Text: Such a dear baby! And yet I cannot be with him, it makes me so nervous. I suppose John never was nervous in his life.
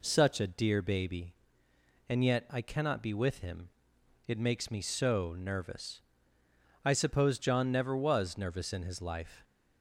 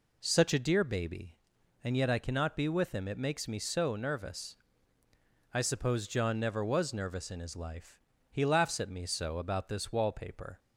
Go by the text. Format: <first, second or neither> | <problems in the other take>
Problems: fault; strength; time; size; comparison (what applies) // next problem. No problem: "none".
first | goes on to say "He laughs at me so about this wallpaper"; strong; from 8.3 s on; 2.2 s long